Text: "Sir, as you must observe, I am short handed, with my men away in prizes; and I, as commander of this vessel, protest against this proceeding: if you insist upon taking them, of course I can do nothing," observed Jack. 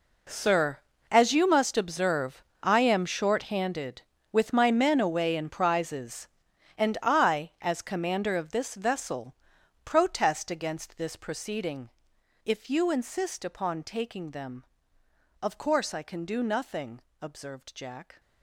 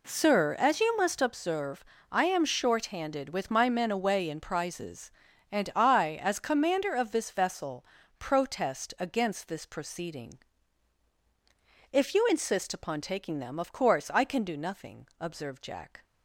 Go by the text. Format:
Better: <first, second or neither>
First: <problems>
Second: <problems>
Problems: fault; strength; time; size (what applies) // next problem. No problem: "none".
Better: second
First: gets quieter; strong; throughout; 15 dB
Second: none